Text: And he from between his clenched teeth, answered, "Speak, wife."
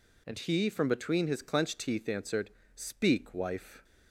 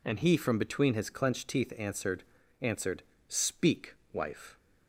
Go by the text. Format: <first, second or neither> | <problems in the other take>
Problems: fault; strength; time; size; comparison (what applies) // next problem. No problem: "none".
first | says "answered" twice; at 2.6 s